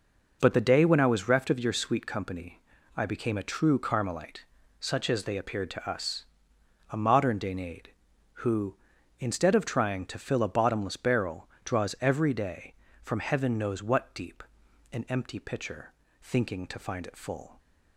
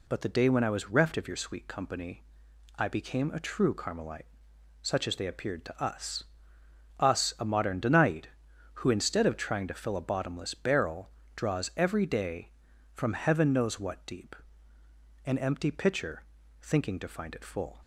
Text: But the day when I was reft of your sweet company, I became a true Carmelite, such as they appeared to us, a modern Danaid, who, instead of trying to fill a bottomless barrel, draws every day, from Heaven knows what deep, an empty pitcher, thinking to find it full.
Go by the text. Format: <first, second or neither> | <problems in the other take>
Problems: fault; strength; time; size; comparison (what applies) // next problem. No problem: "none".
first | says "us" twice; at 6.9 s